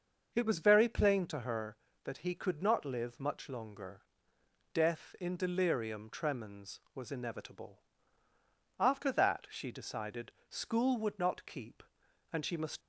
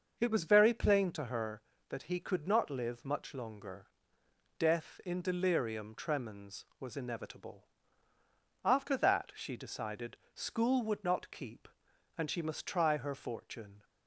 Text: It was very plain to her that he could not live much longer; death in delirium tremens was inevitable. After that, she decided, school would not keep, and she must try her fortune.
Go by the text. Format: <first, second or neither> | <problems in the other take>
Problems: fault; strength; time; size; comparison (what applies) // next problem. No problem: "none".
second | starts louder than the rest; until 1.3 s; 6.5 dB; also in the second // stops before "try her fortune"; at 12.8 s